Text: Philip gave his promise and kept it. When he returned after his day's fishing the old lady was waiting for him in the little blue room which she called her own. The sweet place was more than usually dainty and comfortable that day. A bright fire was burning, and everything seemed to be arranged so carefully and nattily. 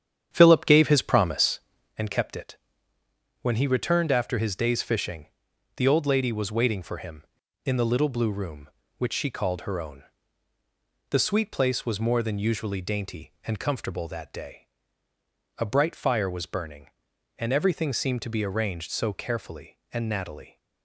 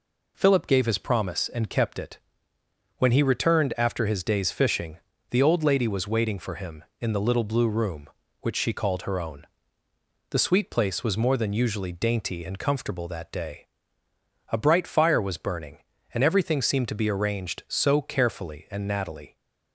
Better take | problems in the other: second | starts louder than the rest; strong; until 2.0 s; 9 dB // pauses between "fishing" and "the"; noticeable; at 5.2 s; 0.50 s long; slight in the second

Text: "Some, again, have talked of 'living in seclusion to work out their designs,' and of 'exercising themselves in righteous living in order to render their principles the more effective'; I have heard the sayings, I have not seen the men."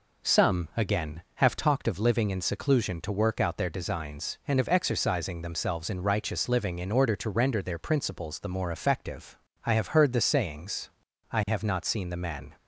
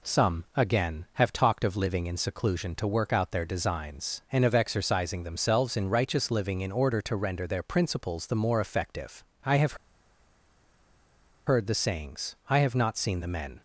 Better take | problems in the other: first | pauses between "have" and "heard"; strong; at 9.7 s; 1.7 s long

